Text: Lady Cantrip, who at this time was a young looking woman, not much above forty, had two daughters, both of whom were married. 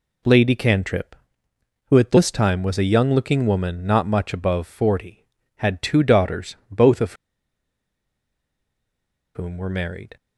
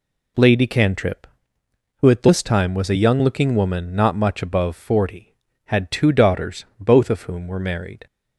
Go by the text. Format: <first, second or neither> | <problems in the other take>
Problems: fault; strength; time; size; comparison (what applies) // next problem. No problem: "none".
second | pauses between "of" and "whom"; strong; at 7.1 s; 2.2 s long